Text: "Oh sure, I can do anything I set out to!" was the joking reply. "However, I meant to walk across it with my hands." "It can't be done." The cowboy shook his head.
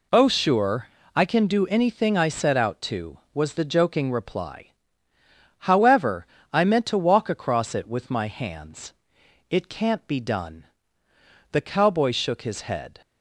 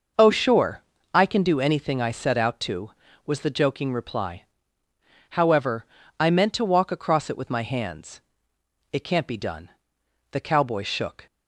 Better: first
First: none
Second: starts louder than the rest; noticeable; until 1.4 s; 6 dB // stops before "his head"; at 11.2 s

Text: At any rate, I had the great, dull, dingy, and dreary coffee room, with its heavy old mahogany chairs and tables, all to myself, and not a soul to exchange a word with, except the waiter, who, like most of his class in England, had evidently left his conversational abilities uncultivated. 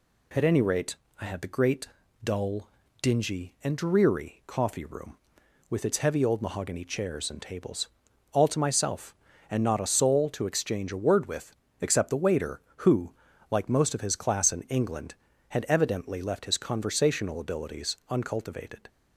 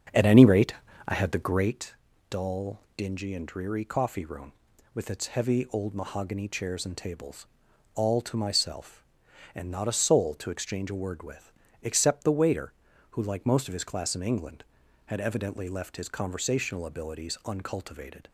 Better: first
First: none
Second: starts louder than the rest; strong; until 1.8 s; 7.5 dB

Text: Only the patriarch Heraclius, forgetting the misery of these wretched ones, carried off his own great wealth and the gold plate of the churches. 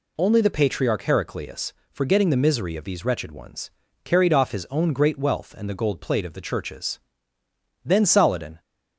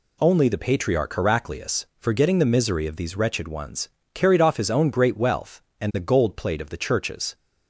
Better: second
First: goes on to say "Then Saladin"; noticeable; from 7.8 s on; 0.76 s long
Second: none

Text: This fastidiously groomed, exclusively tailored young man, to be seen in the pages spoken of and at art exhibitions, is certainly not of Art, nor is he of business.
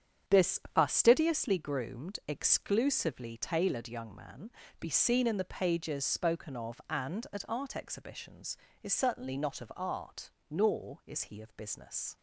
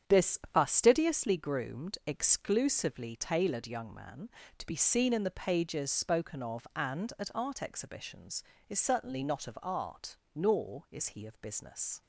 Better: second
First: starts louder than the rest; strong; until 1.4 s; 8 dB // pauses between "This" and "fastidiously"; slight; at 0.5 s; 0.16 s long // skips "to"; at 4.6 s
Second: starts louder than the rest; strong; until 1.2 s; 8 dB // pauses between "This" and "fastidiously"; slight; at 0.3 s; 0.16 s long

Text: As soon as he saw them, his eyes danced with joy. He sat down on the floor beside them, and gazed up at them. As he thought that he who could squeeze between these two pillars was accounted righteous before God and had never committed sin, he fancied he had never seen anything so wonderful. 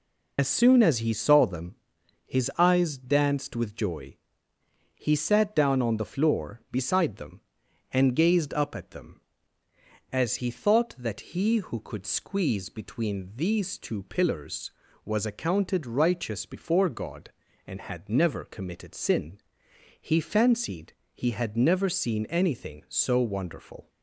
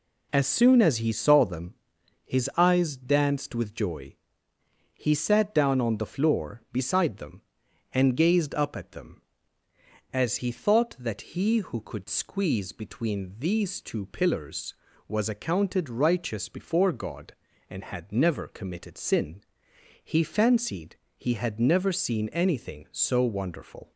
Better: second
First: loses the start of "As"; at 0.3 s; 65 ms // pauses between "fancied" and "he"; slight; at 20.9 s; 0.22 s long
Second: pauses between "fancied" and "he"; slight; at 20.9 s; 0.22 s long

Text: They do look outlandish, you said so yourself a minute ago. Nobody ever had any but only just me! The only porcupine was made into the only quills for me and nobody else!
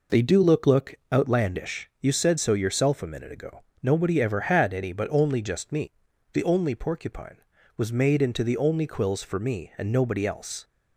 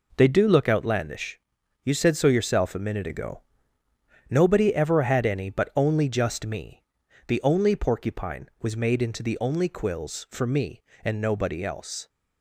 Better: second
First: says "look" twice; at 0.6 s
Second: none

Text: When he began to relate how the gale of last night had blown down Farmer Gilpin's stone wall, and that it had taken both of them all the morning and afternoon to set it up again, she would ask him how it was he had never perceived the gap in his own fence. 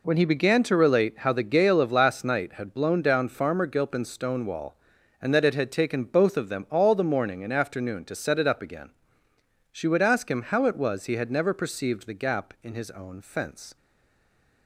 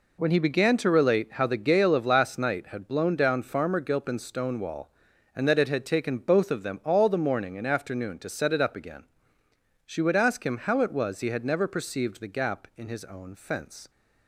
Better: second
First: stays silent after the last word; slight; from 13.7 s on; 0.9 s long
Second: none

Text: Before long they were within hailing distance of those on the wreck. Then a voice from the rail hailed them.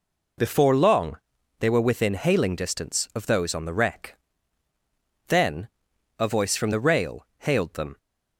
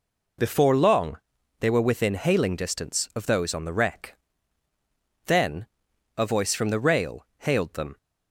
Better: neither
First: pauses between "long" and "they"; at 1.1 s; 0.42 s long // pauses between "Then" and "a"; noticeable; at 5.6 s; 0.50 s long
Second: pauses between "long" and "they"; at 1.1 s; 0.42 s long // pauses between "Then" and "a"; noticeable; at 5.6 s; 0.50 s long

